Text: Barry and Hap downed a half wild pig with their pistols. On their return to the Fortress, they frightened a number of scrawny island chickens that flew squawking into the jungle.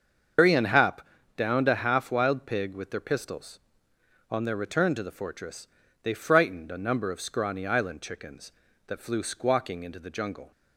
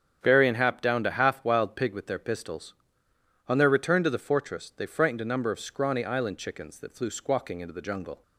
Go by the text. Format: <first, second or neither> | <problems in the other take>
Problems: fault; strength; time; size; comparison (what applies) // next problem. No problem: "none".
second | loses the start of "Barry"; at 0.3 s; 135 ms // starts louder than the rest; until 1.7 s; 7 dB; strong in the second // pauses between "Hap" and "downed"; slight; at 1.0 s; 0.36 s long